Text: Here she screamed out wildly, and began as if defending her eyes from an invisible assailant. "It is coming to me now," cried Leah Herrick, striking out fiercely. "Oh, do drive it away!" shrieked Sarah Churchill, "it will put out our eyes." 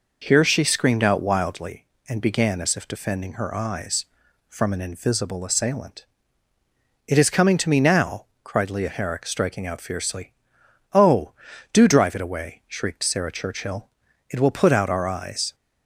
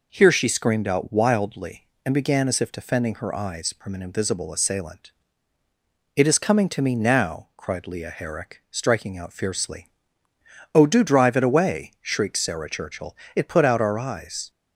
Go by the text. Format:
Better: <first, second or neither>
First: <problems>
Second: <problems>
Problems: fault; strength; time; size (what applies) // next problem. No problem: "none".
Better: first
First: none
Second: skips "will"; at 13.4 s